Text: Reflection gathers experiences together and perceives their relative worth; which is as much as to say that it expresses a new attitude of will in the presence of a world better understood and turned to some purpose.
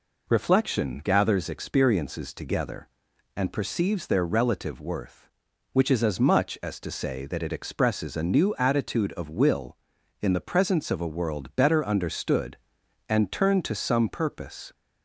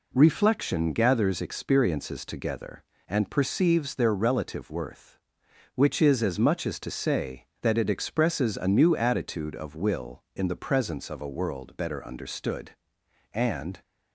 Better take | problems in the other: first | stops before "turned to some purpose"; at 13.8 s

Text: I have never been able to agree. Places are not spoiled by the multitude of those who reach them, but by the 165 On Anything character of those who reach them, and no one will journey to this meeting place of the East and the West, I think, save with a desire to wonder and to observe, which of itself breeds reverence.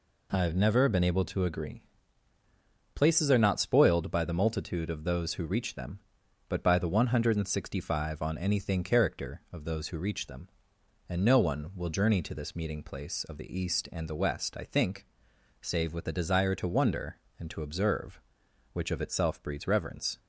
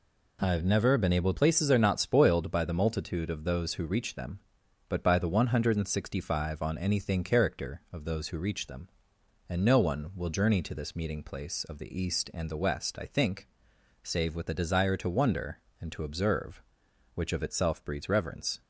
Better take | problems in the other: first | skips "to agree"; at 1.3 s

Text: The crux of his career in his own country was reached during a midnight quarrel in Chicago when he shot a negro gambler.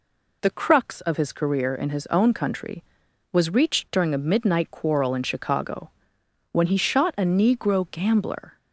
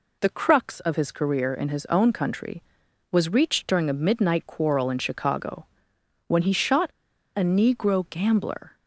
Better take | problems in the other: first | pauses between "Chicago" and "when"; noticeable; at 5.6 s; 0.60 s long; noticeable in the first // pauses between "shot" and "a"; noticeable; at 6.8 s; 0.47 s long

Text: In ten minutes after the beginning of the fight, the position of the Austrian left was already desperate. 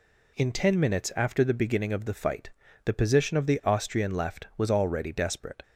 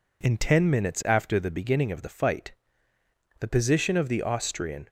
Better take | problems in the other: first | stops before "left was already desperate"; at 4.8 s

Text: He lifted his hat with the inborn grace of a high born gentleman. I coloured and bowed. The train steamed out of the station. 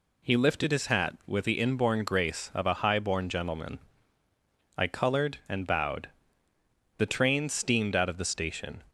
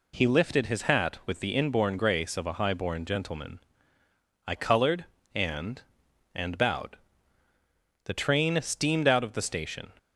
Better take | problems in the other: first | says "and" twice; at 6.3 s

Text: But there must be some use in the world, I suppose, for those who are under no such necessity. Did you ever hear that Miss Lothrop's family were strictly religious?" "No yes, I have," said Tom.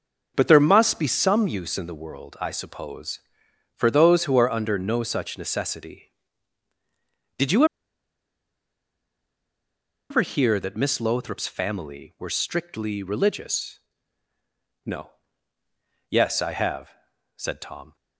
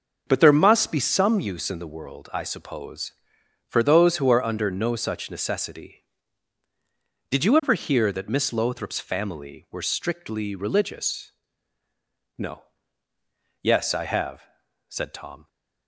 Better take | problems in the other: second | starts louder than the rest; until 1.3 s; 6.5 dB; also in the second // pauses between "you" and "ever"; strong; at 7.6 s; 2.4 s long // pauses between "No" and "yes"; at 15.0 s; 1.0 s long; also in the second

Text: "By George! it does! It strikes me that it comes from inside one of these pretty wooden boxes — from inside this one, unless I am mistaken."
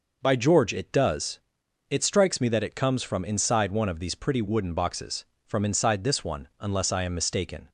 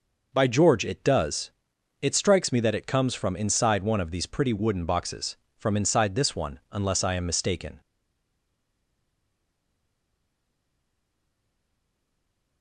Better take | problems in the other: first | stays silent after the last word; strong; from 7.8 s on; 4.8 s long

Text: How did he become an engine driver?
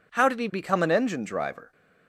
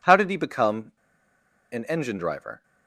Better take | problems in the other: first | pauses between "become" and "an"; noticeable; at 0.9 s; 0.79 s long

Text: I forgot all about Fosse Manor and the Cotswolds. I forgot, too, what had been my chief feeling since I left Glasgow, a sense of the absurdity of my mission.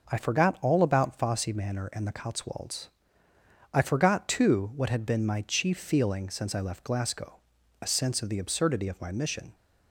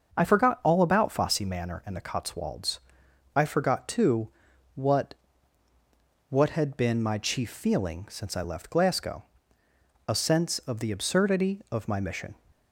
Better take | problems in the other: first | starts louder than the rest; until 1.2 s; 6.5 dB // says "what" twice; at 6.2 s

